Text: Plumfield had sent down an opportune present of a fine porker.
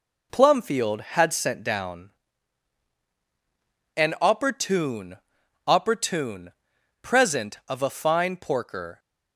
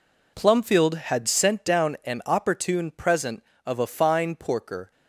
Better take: second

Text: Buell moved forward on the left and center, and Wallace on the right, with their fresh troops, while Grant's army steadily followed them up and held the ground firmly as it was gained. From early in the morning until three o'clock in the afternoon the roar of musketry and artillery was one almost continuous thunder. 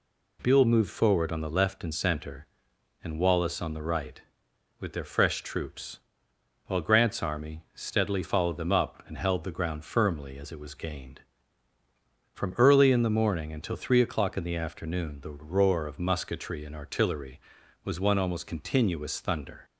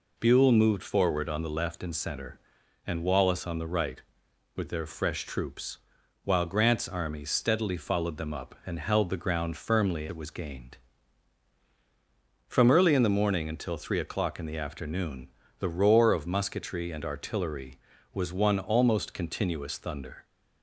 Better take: first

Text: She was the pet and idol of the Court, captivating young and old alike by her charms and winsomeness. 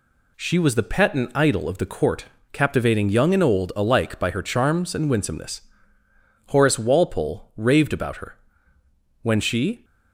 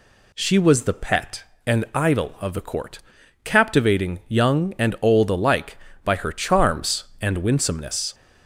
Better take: second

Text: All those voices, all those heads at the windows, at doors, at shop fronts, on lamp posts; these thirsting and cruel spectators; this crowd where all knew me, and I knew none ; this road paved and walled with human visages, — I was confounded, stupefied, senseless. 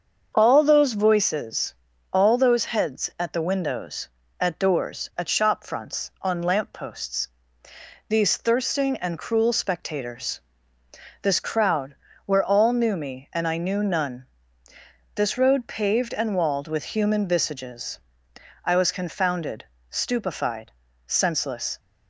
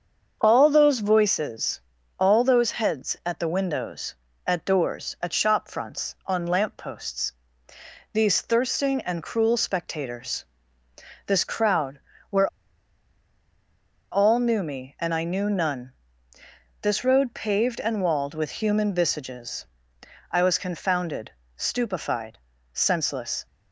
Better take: first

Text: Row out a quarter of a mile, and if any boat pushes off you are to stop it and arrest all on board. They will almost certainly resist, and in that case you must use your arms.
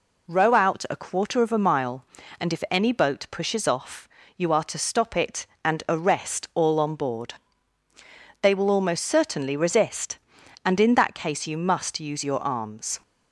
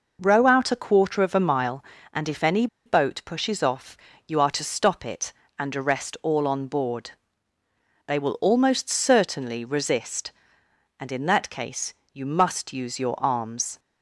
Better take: first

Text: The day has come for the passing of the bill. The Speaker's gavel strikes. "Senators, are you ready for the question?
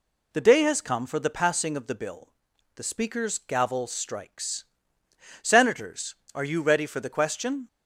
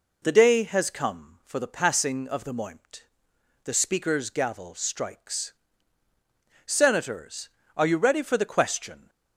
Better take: first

